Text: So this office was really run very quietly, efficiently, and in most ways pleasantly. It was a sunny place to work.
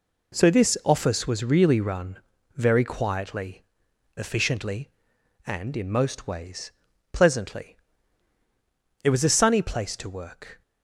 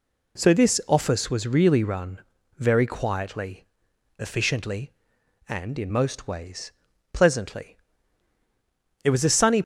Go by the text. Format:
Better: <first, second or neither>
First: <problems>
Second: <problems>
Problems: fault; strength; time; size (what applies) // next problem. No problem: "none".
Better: first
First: pauses between "run" and "very"; at 2.1 s; 0.40 s long // pauses between "ways" and "pleasantly"; at 6.7 s; 0.40 s long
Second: pauses between "run" and "very"; at 2.1 s; 0.40 s long // pauses between "ways" and "pleasantly"; at 6.7 s; 0.40 s long // stops before "place to work"; at 9.6 s